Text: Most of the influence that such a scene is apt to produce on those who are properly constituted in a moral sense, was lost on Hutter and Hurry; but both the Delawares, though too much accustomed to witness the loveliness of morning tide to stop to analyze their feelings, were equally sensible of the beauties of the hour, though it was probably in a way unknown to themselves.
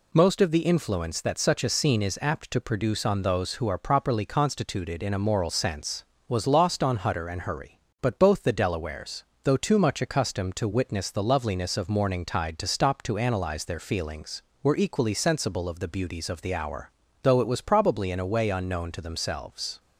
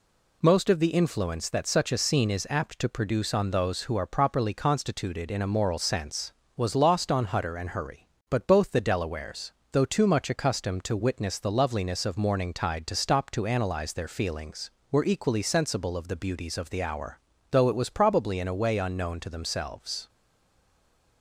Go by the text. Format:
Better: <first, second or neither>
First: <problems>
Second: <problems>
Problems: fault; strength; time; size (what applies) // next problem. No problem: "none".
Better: first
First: none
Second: stays silent after the last word; from 20.0 s on; 1.2 s long